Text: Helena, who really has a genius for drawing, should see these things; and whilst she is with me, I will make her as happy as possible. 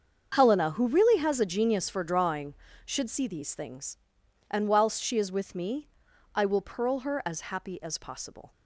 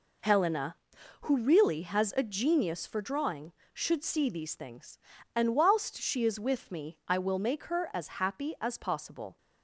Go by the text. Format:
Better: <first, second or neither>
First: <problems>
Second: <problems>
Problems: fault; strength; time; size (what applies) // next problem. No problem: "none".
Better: second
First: starts louder than the rest; until 1.3 s; 7 dB // says "pearl" for "make"; at 6.6 s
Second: none